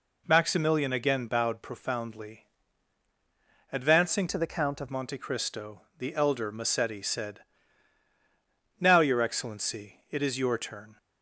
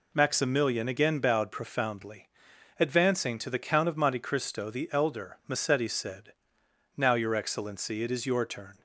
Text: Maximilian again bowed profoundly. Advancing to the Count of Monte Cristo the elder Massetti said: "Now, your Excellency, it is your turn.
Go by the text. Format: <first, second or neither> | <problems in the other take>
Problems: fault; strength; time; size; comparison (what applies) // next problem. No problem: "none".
second | changes voice from "to" to "of"; from 4.2 to 4.8 s; 0.6 s long // pauses between "Cristo" and "the"; slight; at 5.8 s; 0.18 s long